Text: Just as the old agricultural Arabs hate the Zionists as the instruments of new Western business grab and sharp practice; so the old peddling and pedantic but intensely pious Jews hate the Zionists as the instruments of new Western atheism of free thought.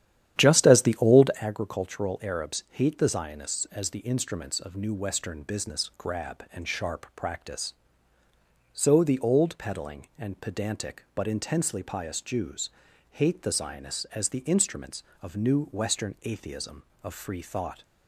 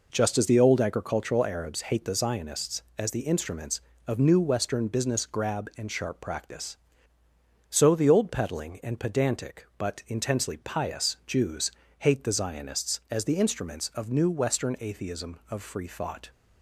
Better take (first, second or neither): second